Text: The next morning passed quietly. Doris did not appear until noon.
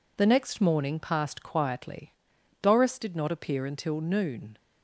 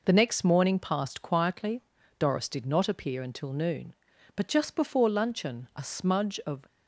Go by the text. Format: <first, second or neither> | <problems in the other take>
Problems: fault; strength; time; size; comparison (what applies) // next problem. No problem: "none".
first | goes on to say "But just before luncheon a smudge of"; strong; from 4.3 s on; 2.3 s long